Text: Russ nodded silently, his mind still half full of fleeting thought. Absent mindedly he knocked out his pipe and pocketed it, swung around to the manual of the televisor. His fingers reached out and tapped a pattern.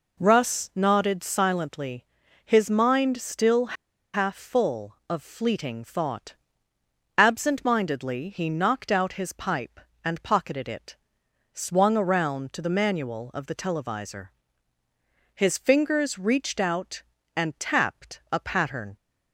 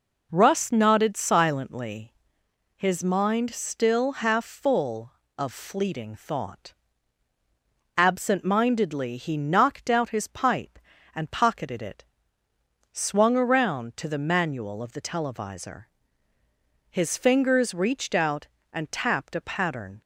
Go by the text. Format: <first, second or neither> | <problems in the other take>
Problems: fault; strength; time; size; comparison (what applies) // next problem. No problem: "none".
second | pauses between "still" and "half"; at 3.7 s; 0.40 s long